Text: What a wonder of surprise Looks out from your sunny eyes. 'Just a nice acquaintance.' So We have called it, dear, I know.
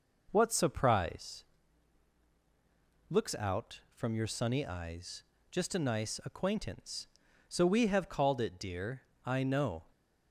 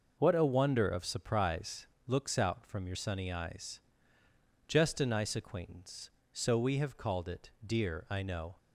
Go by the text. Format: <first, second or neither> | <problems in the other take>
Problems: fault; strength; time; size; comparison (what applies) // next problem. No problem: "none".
second | skips "a wonder of"; at 0.5 s // pauses between "surprise" and "Looks"; strong; at 1.4 s; 1.6 s long; slight in the second